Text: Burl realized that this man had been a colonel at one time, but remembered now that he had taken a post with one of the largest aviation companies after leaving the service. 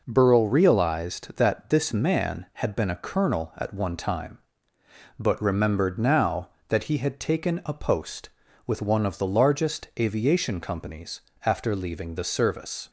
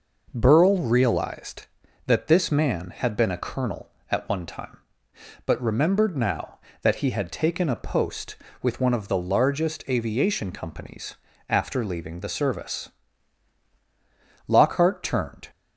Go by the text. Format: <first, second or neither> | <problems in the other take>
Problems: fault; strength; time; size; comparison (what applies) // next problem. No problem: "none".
first | pauses between "companies" and "after"; slight; at 11.1 s; 0.34 s long; slight in the first // goes on to say "Lockhart turned"; noticeable; from 14.4 s on; 1.0 s long